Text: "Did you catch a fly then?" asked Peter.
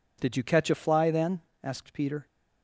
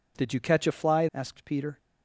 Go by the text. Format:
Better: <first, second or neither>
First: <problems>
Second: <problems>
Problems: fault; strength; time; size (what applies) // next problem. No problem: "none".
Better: first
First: none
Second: skips "then"; at 1.1 s